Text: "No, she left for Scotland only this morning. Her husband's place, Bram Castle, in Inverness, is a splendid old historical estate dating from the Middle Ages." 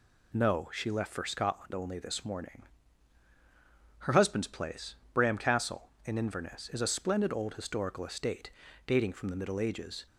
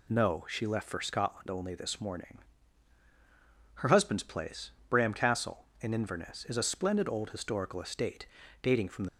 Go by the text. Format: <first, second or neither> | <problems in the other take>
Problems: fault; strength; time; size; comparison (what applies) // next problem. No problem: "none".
first | pauses between "estate" and "dating"; slight; at 8.2 s; 0.36 s long; slight in the first // stops before "Middle Ages"; at 9.0 s